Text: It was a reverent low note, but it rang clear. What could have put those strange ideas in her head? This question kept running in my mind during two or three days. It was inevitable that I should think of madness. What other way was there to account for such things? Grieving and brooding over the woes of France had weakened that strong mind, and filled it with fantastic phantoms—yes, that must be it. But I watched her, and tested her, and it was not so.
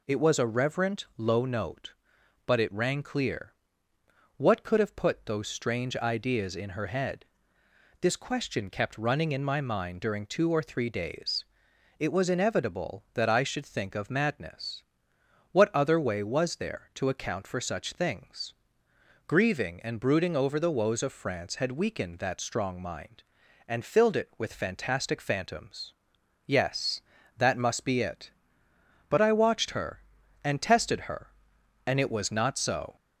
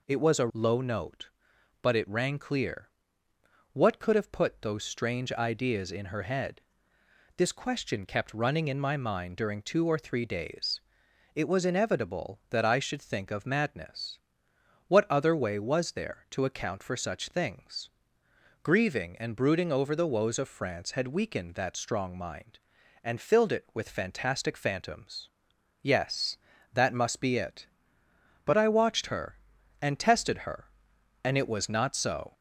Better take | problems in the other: first | skips "reverent"; at 0.5 s

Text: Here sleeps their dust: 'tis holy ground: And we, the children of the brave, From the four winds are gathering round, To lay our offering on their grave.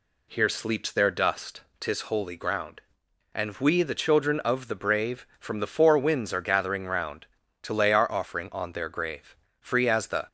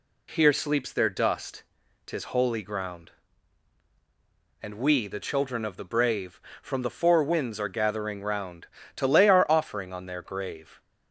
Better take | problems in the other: second | goes on to say "Free as the"; noticeable; from 9.5 s on; 0.68 s long

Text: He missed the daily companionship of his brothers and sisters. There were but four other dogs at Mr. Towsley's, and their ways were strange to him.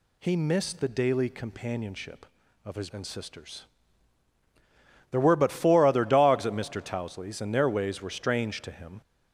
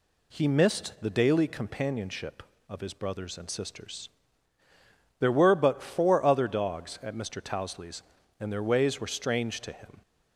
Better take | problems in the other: second | skips "brothers"; at 2.9 s

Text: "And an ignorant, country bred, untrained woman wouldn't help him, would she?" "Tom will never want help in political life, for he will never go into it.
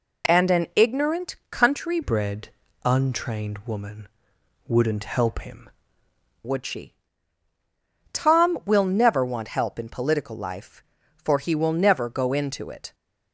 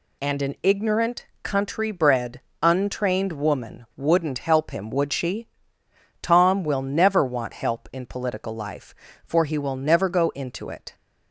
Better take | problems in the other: second | changes voice from "bred" to "him"; from 2.0 to 5.6 s; 3.6 s long // pauses between "woman" and "wouldn't"; noticeable; at 4.0 s; 0.60 s long

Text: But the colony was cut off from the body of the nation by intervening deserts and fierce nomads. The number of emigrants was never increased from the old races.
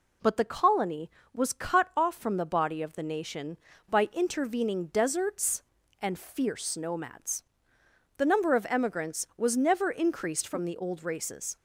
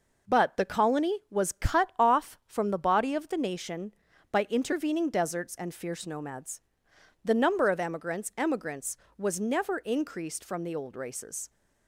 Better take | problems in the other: first | says "emigrants" twice; at 8.3 s

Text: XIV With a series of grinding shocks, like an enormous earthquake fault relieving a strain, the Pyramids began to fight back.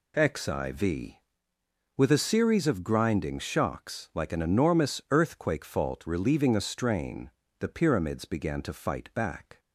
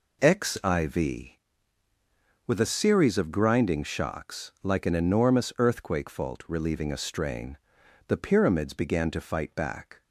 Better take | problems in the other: neither | none

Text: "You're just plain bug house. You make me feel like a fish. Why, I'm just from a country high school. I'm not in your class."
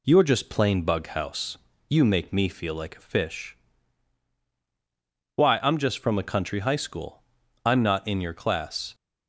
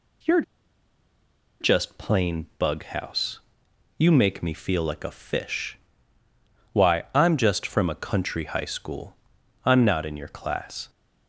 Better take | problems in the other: first | pauses between "You're" and "just"; at 0.4 s; 1.1 s long

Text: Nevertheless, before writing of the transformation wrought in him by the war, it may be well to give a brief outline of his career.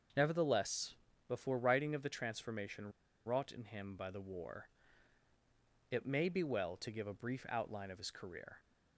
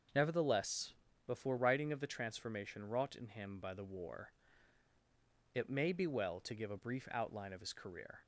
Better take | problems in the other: second | starts louder than the rest; until 1.5 s; 6.5 dB; also in the second // pauses between "transformation" and "wrought"; slight; at 2.9 s; 0.34 s long

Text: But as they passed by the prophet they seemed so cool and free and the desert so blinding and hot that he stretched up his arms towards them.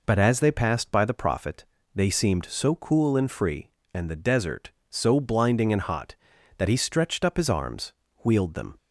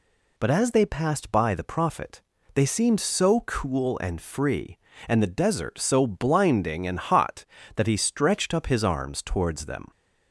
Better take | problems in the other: second | pauses between "prophet" and "they"; slight; at 1.6 s; 0.32 s long; slight in the second // says "wheeled" for "towards"; at 8.2 s

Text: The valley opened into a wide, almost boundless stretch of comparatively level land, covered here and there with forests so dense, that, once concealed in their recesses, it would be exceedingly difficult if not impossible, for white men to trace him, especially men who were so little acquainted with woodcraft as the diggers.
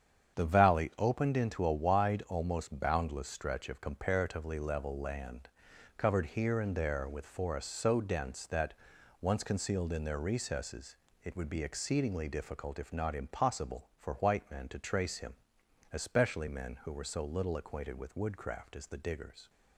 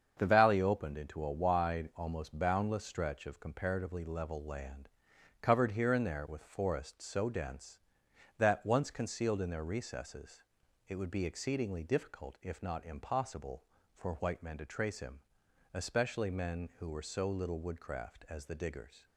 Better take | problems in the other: first | starts louder than the rest; until 1.1 s; 7 dB; strong in the first // skips "acquainted with"; at 17.6 s

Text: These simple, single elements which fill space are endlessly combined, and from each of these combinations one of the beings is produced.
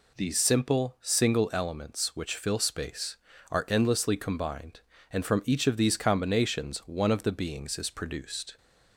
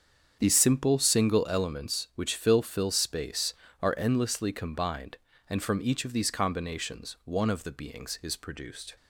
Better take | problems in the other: first | starts louder than the rest; strong; until 1.4 s; 7.5 dB // says "fill" twice; at 2.6 s

